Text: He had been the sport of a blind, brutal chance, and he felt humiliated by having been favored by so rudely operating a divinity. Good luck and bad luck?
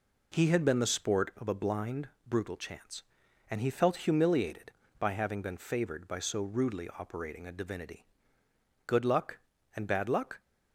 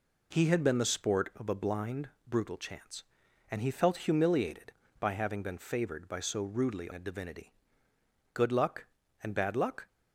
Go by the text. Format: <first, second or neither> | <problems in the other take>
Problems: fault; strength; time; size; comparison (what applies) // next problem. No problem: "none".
first | skips "operating"; at 6.9 s